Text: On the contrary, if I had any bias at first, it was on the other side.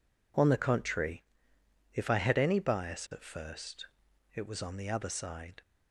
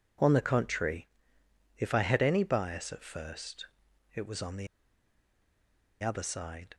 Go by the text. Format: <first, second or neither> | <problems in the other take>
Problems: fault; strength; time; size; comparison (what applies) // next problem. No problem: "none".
first | pauses between "the" and "other"; strong; at 4.6 s; 1.3 s long